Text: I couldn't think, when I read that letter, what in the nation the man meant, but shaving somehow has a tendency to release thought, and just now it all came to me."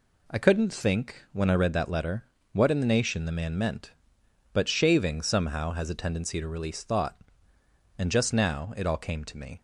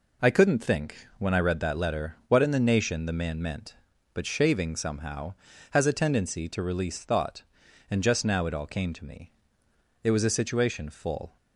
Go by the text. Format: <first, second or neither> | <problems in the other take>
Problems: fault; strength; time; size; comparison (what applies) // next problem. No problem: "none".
first | goes on to say "It was a situation full"; from 10.0 s on; 1.3 s long